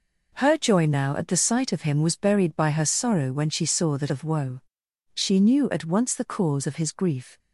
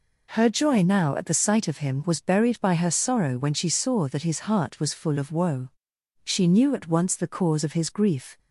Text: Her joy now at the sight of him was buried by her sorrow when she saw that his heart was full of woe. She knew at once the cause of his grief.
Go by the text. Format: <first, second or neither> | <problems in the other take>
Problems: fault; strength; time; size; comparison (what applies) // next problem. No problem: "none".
second | skips "his heart was full"; at 4.0 s